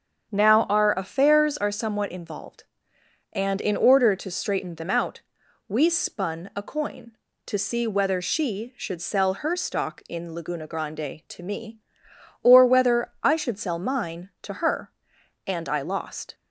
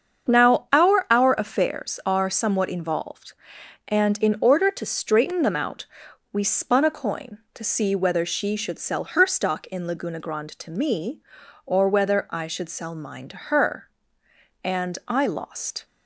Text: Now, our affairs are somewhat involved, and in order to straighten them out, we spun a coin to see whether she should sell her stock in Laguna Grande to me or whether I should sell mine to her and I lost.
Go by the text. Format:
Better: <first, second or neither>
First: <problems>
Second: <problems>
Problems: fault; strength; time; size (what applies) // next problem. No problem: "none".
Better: first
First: starts louder than the rest; until 1.3 s; 7 dB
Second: starts louder than the rest; strong; until 1.3 s; 7 dB // says "our" twice; at 1.0 s